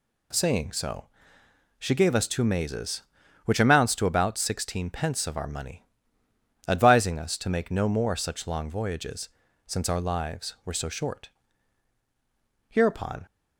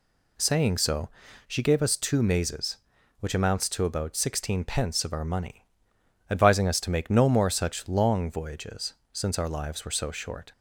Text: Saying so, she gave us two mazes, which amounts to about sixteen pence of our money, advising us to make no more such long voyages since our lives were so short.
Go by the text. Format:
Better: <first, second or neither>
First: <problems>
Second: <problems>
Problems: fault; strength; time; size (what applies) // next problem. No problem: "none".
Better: second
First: pauses between "voyages" and "since"; at 9.2 s; 0.38 s long // goes on to say "Hereupon"; from 12.6 s on; 0.56 s long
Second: pauses between "voyages" and "since"; slight; at 8.9 s; 0.20 s long